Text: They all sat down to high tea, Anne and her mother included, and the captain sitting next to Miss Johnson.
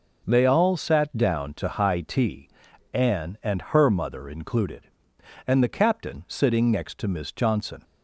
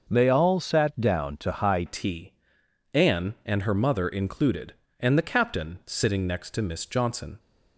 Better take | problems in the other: first | changes voice at "tea"; from 1.8 s on; 5.5 s long

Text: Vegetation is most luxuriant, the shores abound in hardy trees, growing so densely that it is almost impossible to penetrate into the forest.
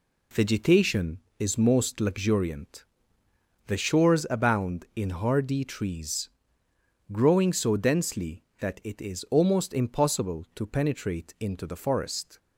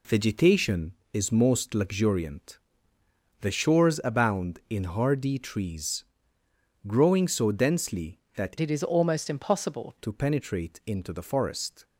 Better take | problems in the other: first | changes voice from "it" to "impossible"; from 8.5 to 9.9 s; 1.4 s long

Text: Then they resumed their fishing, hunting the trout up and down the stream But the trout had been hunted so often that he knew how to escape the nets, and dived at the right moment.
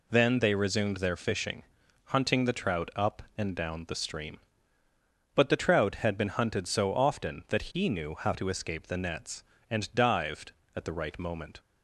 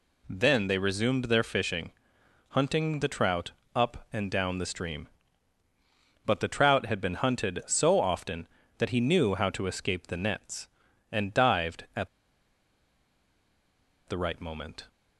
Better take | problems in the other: first | pauses between "trout" and "up"; slight; at 3.5 s; 0.24 s long // pauses between "at" and "the"; strong; at 12.0 s; 1.9 s long

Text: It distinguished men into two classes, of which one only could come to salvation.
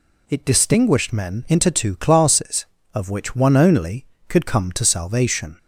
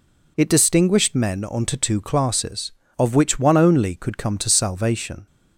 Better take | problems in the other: first | says "onto" for "into"; at 1.4 s

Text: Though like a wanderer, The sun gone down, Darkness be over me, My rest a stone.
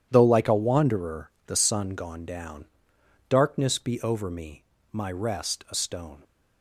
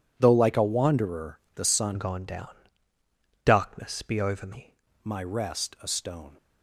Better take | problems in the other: first | changes voice from "gone" to "me"; from 1.9 to 4.7 s; 2.8 s long

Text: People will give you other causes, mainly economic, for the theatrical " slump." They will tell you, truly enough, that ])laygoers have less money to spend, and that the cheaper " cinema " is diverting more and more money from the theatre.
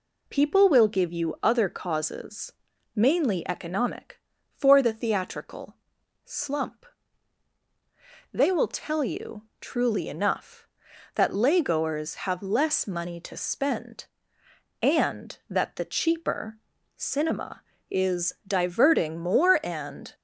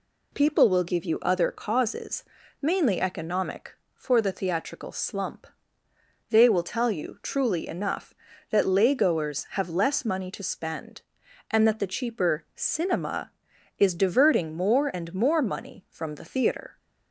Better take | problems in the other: second | pauses between "is" and "diverting"; slight; at 18.3 s; 0.16 s long // stops before "more money from the theatre"; at 20.1 s

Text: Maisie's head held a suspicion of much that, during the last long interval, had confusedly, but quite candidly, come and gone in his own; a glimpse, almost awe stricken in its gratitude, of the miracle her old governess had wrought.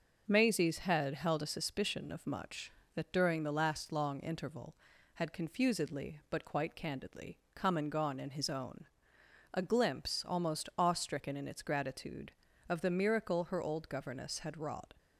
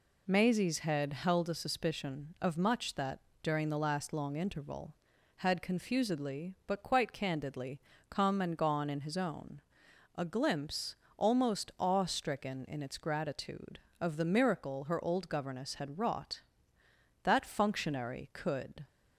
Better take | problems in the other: first | goes on to say "That functionary could"; from 17.2 s on; 1.6 s long

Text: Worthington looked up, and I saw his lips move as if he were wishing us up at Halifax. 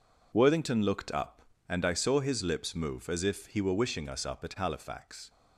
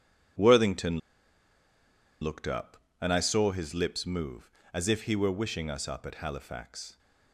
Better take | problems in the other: first | pauses between "Worthington" and "looked"; at 0.9 s; 1.2 s long

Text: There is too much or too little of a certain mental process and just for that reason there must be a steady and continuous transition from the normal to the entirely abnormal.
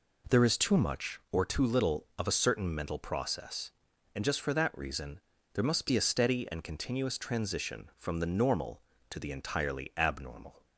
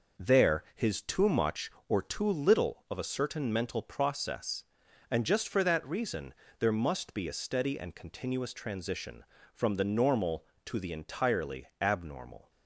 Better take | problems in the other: first | says "his" for "is"; at 0.7 s // pauses between "reason" and "there"; slight; at 6.3 s; 0.26 s long; slight in the first // pauses between "entirely" and "abnormal"; slight; at 11.6 s; 0.16 s long

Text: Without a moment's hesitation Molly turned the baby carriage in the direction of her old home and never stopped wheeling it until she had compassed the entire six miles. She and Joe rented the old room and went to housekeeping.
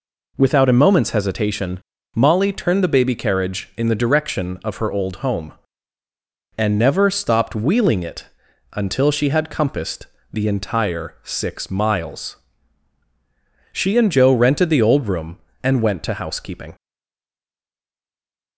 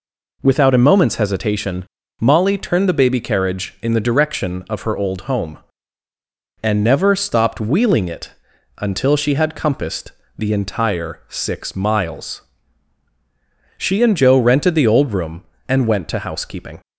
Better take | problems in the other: second | pauses between "hesitation" and "Molly"; slight; at 1.7 s; 0.36 s long; slight in the second // pauses between "it" and "until"; noticeable; at 8.2 s; 0.48 s long; noticeable in the second // pauses between "compassed" and "the"; slight; at 10.0 s; 0.26 s long; slight in the second // stays silent after the last word; noticeable; from 16.7 s on; 1.8 s long

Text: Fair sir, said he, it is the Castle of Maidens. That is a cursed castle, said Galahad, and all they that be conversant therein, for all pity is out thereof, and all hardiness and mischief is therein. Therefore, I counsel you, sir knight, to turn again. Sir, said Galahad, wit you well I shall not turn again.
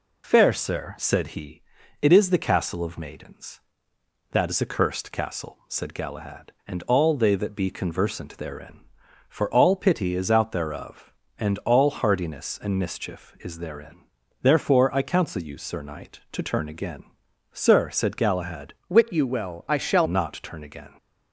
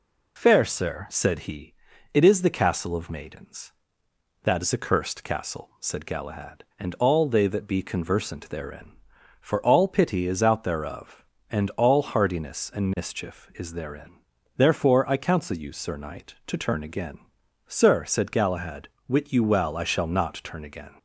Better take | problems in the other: second | changes voice from "wit" to "shall"; from 18.8 to 20.0 s; 1.2 s long

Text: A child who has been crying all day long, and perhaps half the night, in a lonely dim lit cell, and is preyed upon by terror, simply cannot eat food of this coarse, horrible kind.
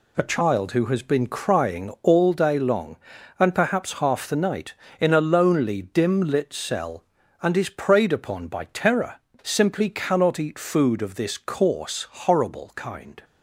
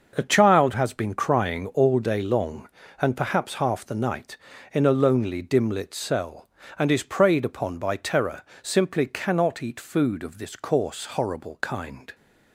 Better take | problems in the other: first | starts louder than the rest; until 1.1 s; 6 dB // skips "who"; at 0.7 s

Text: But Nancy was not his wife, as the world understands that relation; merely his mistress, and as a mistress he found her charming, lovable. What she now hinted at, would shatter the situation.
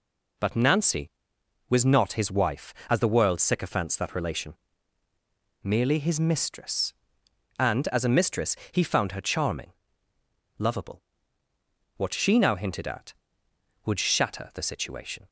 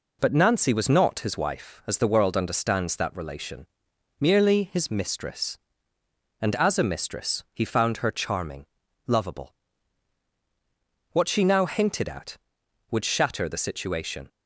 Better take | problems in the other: second | says "sycophants" for "understands"; at 3.3 s // pauses between "mistress" and "he"; slight; at 8.5 s; 0.18 s long

